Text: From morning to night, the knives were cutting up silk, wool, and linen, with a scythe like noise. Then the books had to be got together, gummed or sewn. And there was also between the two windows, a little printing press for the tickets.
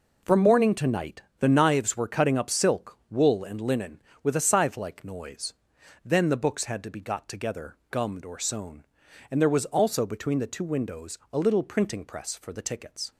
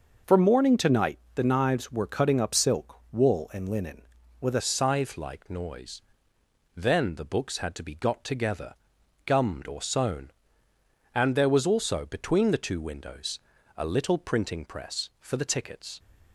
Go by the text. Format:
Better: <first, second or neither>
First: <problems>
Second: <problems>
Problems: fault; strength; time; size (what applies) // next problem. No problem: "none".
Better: first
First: none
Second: changes voice at "scythe"; from 4.6 s on; 11.3 s long